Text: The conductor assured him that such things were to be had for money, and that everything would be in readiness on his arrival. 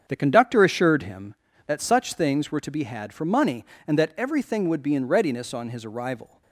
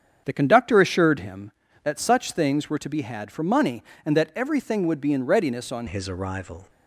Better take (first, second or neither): first